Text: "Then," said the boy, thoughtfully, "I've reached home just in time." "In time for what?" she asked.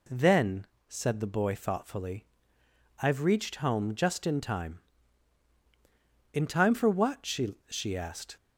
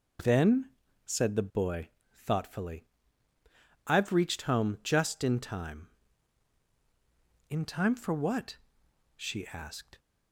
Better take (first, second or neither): second